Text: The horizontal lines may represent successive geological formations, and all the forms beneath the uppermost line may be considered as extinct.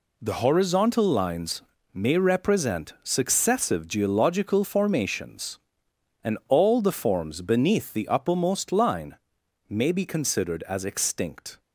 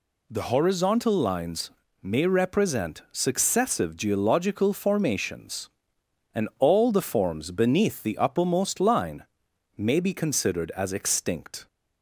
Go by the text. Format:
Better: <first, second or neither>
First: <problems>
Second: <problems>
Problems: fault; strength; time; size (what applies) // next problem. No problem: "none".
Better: second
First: gets quieter; strong; throughout; 8 dB // pauses between "lines" and "may"; slight; at 1.6 s; 0.32 s long // pauses between "line" and "may"; noticeable; at 9.1 s; 0.52 s long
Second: pauses between "lines" and "may"; slight; at 1.6 s; 0.32 s long // pauses between "line" and "may"; noticeable; at 9.2 s; 0.52 s long